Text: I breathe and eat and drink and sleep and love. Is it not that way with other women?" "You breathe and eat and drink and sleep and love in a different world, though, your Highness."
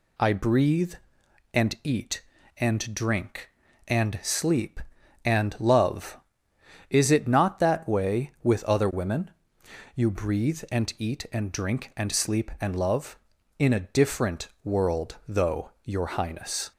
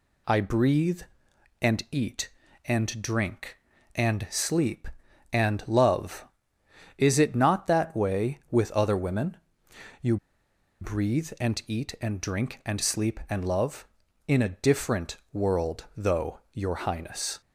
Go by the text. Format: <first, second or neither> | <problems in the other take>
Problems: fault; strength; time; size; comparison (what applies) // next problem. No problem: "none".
first | pauses between "You" and "breathe"; noticeable; at 10.1 s; 0.64 s long // pauses between "different" and "world"; slight; at 15.1 s; 0.16 s long; slight in the first